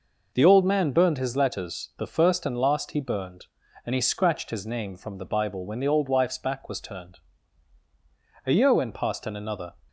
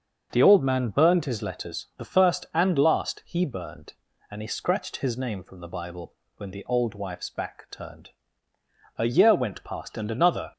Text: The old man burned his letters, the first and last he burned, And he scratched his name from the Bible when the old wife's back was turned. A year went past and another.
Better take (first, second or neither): first